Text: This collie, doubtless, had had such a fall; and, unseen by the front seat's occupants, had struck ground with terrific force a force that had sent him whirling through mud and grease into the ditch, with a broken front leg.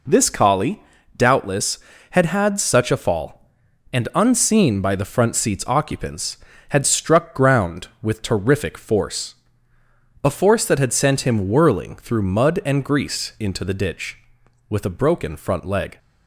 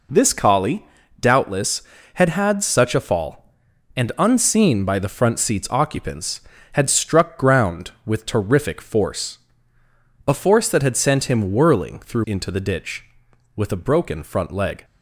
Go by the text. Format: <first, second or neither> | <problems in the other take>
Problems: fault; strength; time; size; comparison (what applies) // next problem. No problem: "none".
first | pauses between "force" and "a"; noticeable; at 9.3 s; 0.88 s long; noticeable in the first // skips "mud and grease"; at 12.2 s